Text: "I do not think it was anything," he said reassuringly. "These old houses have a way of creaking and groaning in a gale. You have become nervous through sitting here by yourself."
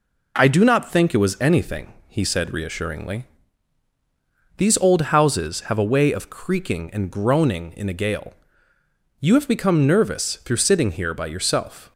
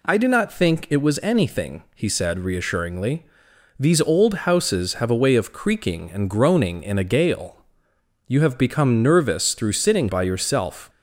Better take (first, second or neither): first